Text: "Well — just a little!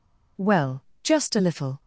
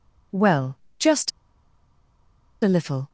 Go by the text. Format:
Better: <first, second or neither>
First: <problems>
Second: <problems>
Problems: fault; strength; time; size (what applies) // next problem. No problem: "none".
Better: first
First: none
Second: pauses between "just" and "a"; strong; at 1.3 s; 1.3 s long